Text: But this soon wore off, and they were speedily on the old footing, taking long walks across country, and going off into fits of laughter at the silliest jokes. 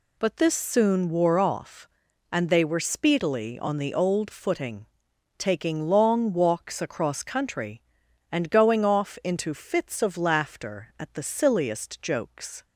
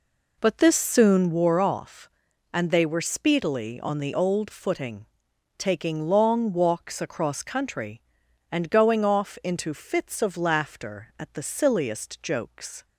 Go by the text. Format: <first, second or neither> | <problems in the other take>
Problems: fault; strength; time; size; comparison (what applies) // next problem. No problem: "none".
first | starts louder than the rest; until 1.5 s; 3.5 dB